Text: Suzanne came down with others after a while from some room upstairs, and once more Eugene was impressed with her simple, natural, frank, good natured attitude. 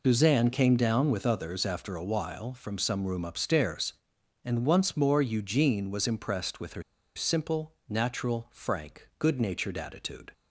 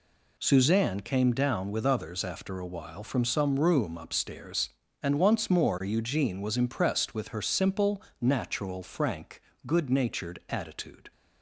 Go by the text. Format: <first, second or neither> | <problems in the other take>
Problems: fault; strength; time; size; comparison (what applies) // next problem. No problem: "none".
second | pauses between "her" and "simple"; slight; at 6.8 s; 0.34 s long